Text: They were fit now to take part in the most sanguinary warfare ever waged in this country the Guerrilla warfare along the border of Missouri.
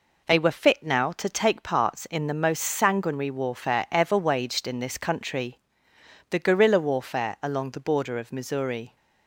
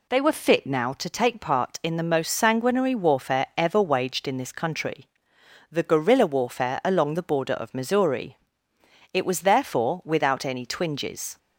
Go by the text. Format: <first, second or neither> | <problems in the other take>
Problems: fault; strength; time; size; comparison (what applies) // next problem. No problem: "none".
first | pauses between "country" and "the"; noticeable; at 5.0 s; 0.64 s long; noticeable in the first // goes on to say "It was therefore without any twinges"; strong; from 9.1 s on; 2.2 s long